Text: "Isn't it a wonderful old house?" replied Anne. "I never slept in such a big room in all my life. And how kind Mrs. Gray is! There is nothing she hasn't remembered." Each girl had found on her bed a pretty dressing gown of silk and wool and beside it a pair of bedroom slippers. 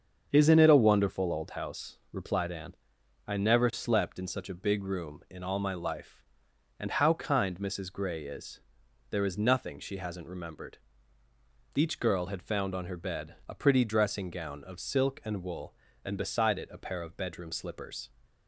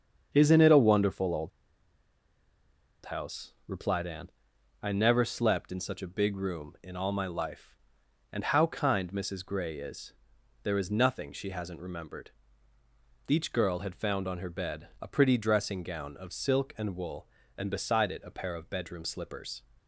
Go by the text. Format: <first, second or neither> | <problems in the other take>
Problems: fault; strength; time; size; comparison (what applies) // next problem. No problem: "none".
first | starts louder than the rest; strong; until 1.3 s; 7.5 dB; strong in the first // pauses between "old" and "house"; strong; at 1.5 s; 1.5 s long